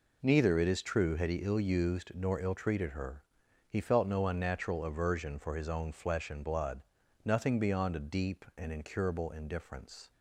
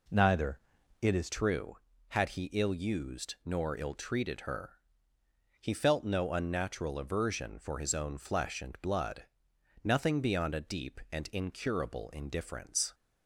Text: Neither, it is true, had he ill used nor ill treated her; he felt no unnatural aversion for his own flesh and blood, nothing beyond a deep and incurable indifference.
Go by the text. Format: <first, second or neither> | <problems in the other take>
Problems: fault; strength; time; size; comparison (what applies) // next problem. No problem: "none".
first | changes voice at "true"; from 1.3 s on; 11.6 s long